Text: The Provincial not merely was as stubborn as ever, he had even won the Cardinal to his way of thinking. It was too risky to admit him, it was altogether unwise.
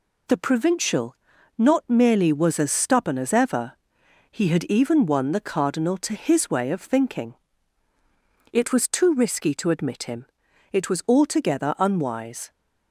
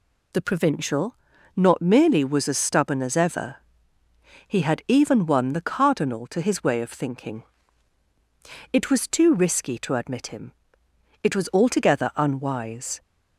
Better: neither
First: pauses between "Provincial" and "not"; at 1.1 s; 0.42 s long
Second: pauses between "Provincial" and "not"; at 1.1 s; 0.40 s long

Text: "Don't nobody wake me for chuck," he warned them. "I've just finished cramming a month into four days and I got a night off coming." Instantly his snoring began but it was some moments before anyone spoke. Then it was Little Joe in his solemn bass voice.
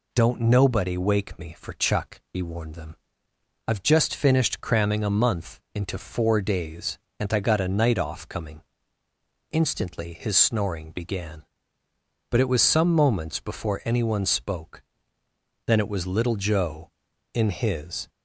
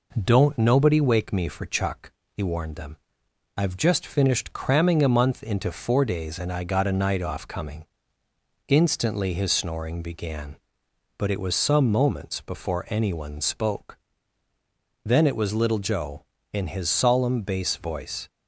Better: second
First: stops before "solemn bass voice"; at 18.0 s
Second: none

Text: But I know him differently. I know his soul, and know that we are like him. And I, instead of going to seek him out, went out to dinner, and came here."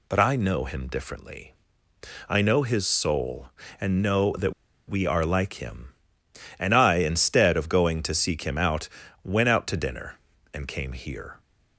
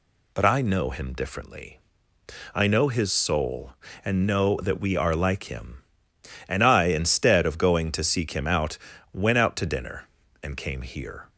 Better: second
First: pauses between "that" and "we"; slight; at 4.5 s; 0.35 s long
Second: none

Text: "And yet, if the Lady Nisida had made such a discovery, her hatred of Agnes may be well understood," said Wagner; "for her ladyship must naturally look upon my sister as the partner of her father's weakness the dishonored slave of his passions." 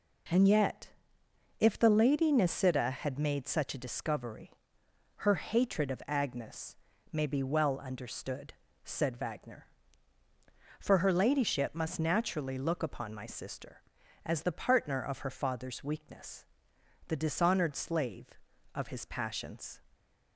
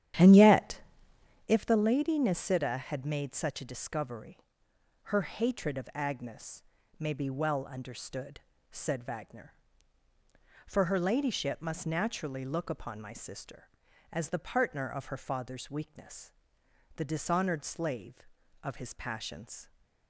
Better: first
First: pauses between "Agnes" and "may"; slight; at 6.7 s; 0.36 s long // pauses between "weakness" and "the"; noticeable; at 16.4 s; 0.62 s long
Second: starts louder than the rest; strong; until 1.6 s; 10.5 dB // pauses between "Agnes" and "may"; slight; at 6.6 s; 0.36 s long // pauses between "weakness" and "the"; noticeable; at 16.2 s; 0.64 s long

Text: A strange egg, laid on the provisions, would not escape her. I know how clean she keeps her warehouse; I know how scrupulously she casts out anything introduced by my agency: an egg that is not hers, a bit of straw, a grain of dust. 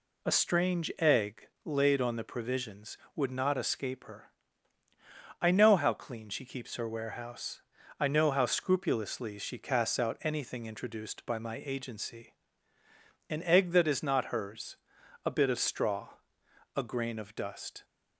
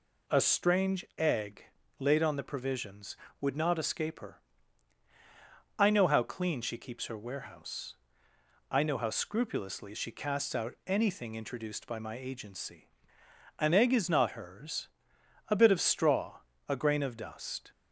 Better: first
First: none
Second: skips "that"; at 13.9 s

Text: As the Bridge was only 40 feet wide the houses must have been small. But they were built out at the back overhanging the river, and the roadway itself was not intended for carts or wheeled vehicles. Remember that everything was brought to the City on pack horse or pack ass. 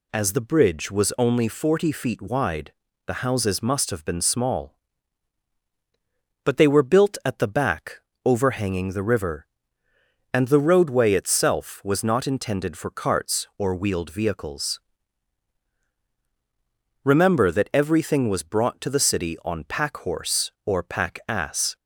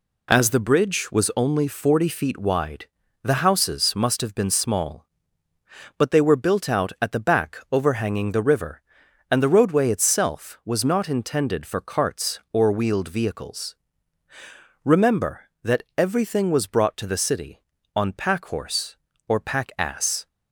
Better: second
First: pauses between "wide" and "the"; slight; at 2.7 s; 0.34 s long // skips "out"; at 7.2 s // pauses between "back" and "overhanging"; slight; at 8.0 s; 0.22 s long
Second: pauses between "wide" and "the"; at 2.8 s; 0.38 s long

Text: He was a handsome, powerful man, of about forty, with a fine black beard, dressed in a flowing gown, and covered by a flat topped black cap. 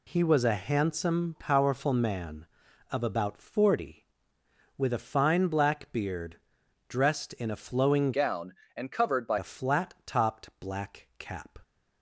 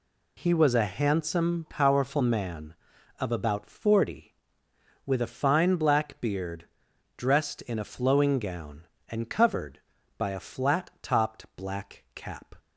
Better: second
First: changes voice from "gown" to "by"; from 8.1 to 9.3 s; 1.2 s long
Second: none

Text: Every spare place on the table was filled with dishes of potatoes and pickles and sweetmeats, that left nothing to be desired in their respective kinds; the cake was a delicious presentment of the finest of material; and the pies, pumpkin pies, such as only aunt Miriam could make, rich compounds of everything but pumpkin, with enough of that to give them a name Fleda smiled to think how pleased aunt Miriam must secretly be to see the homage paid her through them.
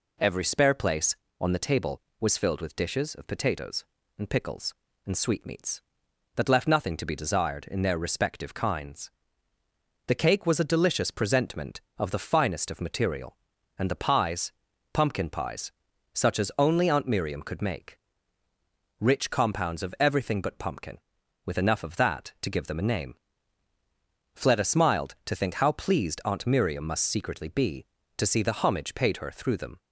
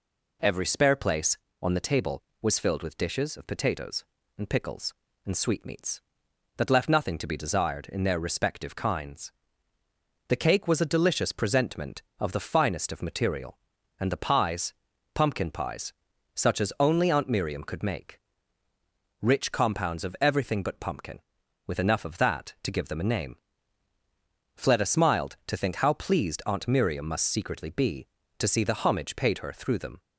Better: neither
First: pauses between "name" and "Fleda"; at 23.1 s; 1.2 s long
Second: pauses between "name" and "Fleda"; at 23.3 s; 1.2 s long

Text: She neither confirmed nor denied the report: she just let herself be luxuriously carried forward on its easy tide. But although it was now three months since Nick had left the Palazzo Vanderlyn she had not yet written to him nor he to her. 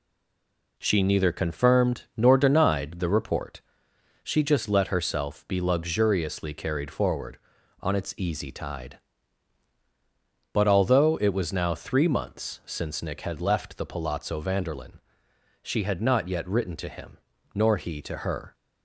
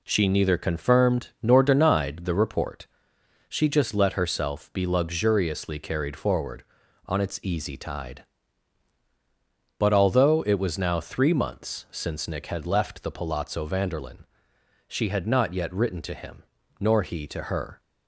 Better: second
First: stays silent before the first word; slight; until 0.7 s; 0.7 s long // pauses between "Vanderlyn" and "she"; noticeable; at 14.9 s; 0.64 s long // pauses between "him" and "nor"; at 17.1 s; 0.38 s long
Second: pauses between "Vanderlyn" and "she"; noticeable; at 14.2 s; 0.64 s long // pauses between "him" and "nor"; at 16.4 s; 0.38 s long

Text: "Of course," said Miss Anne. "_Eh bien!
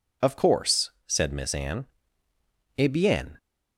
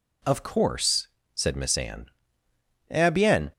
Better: neither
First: none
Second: none

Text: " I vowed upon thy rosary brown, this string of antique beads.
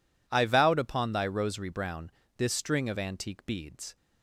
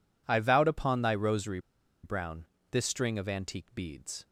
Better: first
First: none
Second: pauses between "rosary" and "brown"; at 1.5 s; 0.44 s long

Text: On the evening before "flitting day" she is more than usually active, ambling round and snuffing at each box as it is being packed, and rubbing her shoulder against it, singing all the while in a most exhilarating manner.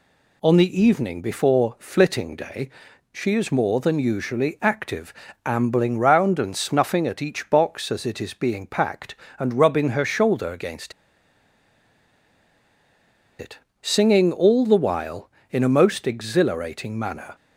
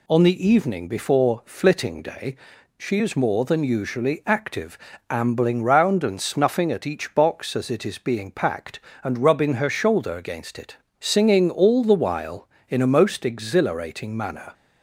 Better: second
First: pauses between "day" and "she"; at 2.6 s; 0.42 s long // pauses between "against" and "it"; strong; at 10.9 s; 2.4 s long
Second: pauses between "day" and "she"; at 2.3 s; 0.40 s long

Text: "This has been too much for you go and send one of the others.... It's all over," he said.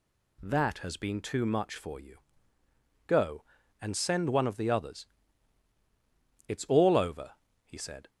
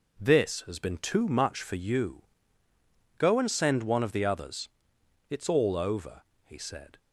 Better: second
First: says "That" for "This"; at 0.4 s // pauses between "you" and "go"; noticeable; at 2.1 s; 0.88 s long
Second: pauses between "you" and "go"; noticeable; at 2.2 s; 0.96 s long

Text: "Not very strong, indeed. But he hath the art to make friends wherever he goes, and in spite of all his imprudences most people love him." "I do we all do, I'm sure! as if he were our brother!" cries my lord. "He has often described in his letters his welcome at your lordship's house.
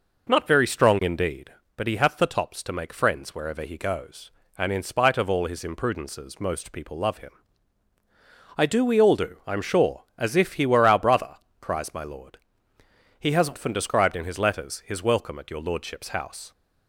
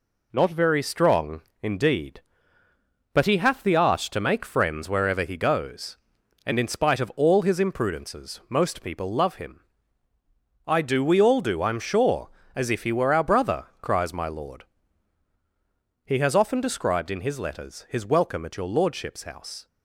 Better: second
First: says "tops" for "art"; at 2.2 s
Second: none

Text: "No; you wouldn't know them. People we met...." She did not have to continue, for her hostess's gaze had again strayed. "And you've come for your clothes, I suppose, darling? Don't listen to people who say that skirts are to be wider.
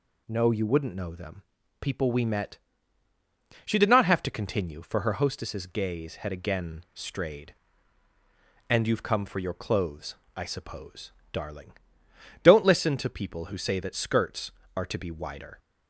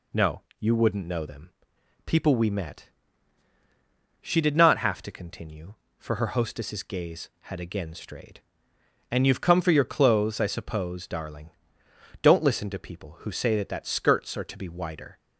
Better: first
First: none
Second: says "that" twice; at 13.7 s

